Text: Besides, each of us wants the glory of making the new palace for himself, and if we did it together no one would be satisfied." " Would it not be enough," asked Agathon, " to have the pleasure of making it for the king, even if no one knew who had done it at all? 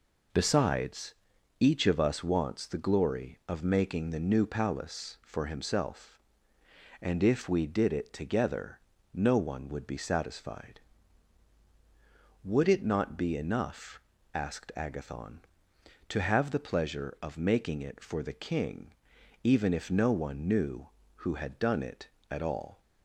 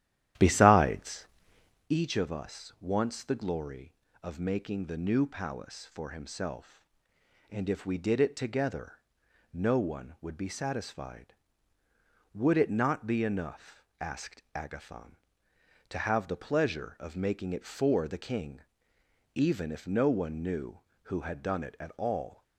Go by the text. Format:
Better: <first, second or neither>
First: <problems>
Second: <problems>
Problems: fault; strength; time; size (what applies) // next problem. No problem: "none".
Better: first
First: pauses between "together" and "no"; slight; at 8.7 s; 0.34 s long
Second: starts louder than the rest; strong; until 1.9 s; 12 dB // pauses between "together" and "no"; noticeable; at 8.9 s; 0.56 s long